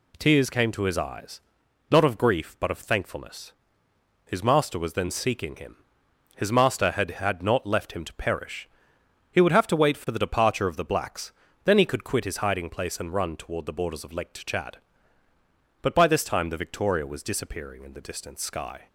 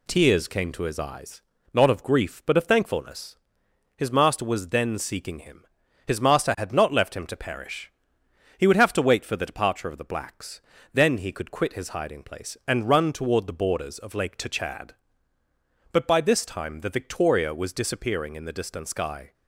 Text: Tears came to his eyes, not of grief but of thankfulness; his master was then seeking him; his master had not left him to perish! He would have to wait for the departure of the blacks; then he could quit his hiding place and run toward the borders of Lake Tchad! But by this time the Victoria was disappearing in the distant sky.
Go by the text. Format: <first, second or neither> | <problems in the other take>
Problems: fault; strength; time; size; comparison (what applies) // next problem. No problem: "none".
second | says "had" twice; at 7.1 s